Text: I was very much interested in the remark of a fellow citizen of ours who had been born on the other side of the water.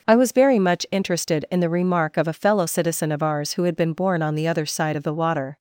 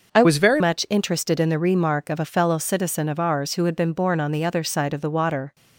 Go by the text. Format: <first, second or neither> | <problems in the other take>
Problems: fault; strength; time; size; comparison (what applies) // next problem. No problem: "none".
first | changes voice from "was" to "very"; from 0.2 to 0.6 s; 0.4 s long